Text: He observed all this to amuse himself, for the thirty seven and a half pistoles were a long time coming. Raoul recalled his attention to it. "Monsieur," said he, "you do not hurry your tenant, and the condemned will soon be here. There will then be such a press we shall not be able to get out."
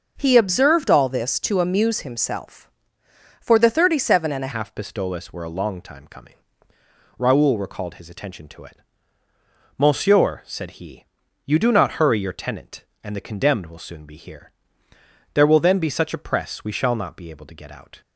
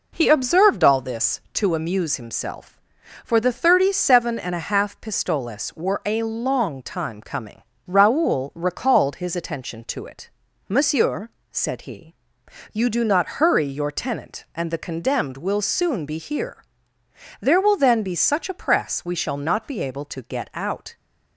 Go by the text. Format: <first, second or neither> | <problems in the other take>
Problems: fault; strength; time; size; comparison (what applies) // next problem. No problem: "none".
second | starts louder than the rest; until 1.1 s; 6.5 dB // changes voice at "half"; from 4.5 s on; 13.5 s long